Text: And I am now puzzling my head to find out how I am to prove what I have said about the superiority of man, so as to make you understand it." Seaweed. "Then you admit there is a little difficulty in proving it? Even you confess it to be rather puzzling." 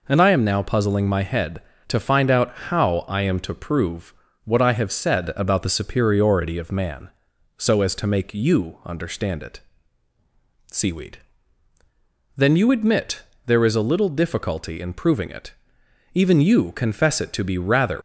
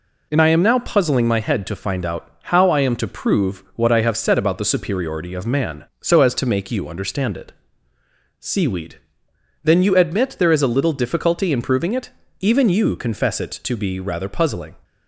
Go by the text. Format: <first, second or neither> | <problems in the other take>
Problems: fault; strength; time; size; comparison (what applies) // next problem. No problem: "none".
second | pauses between "out" and "how"; slight; at 2.5 s; 0.16 s long // pauses between "prove" and "what"; slight; at 4.1 s; 0.32 s long // pauses between "admit" and "there"; slight; at 13.2 s; 0.24 s long // stops before "puzzling"; at 17.9 s